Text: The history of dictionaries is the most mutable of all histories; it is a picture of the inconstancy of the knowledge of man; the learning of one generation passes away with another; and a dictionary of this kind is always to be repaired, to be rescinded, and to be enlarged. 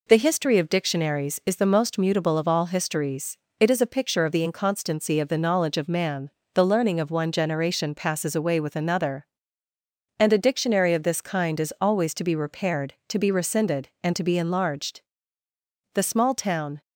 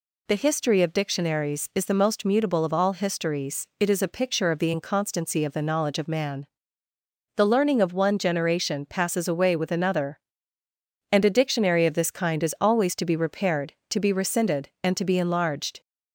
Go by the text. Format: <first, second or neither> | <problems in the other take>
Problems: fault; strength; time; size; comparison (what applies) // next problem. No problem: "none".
second | goes on to say "The small town"; noticeable; from 15.9 s on; 0.88 s long